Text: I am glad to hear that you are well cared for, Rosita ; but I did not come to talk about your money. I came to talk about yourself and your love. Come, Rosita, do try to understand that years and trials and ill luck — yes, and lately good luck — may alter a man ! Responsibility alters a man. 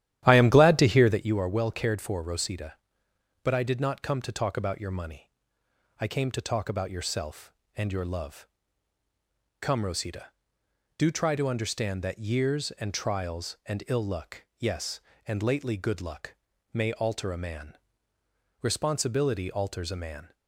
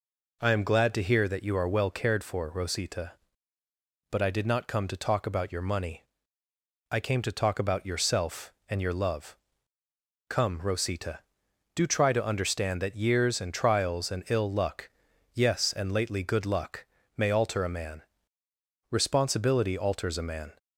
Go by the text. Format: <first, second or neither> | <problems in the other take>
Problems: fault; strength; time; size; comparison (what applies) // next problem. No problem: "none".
second | starts louder than the rest; strong; until 1.2 s; 12.5 dB